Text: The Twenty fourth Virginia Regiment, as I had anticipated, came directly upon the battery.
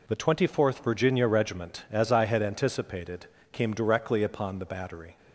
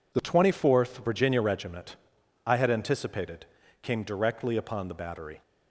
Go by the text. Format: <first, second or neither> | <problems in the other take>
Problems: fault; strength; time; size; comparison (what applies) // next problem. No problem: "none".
first | skips "as"; at 2.2 s